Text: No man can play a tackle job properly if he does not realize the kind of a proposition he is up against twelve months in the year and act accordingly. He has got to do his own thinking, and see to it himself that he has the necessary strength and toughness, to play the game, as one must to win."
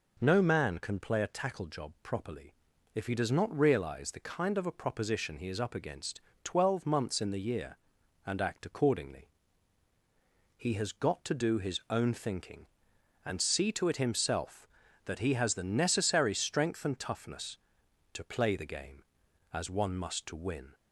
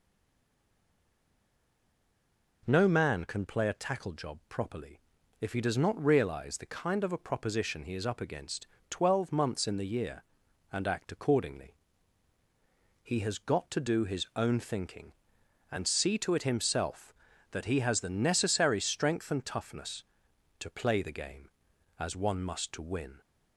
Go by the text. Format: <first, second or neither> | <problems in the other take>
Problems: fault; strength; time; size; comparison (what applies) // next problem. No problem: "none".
first | stays silent before the first word; strong; until 2.6 s; 2.6 s long // pauses between "properly" and "if"; at 5.0 s; 0.40 s long; also in the first // pauses between "against" and "twelve"; slight; at 8.6 s; 0.22 s long; slight in the first